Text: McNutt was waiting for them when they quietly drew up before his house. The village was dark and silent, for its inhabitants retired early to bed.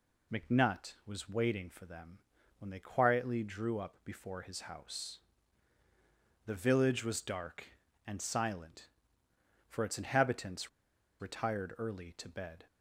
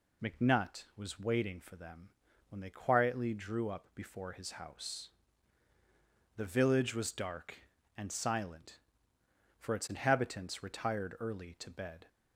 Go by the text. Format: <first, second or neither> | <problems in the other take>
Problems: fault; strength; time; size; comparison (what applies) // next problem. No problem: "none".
second | pauses between "them" and "when"; at 2.1 s; 0.40 s long; also in the second // pauses between "inhabitants" and "retired"; noticeable; at 10.6 s; 0.52 s long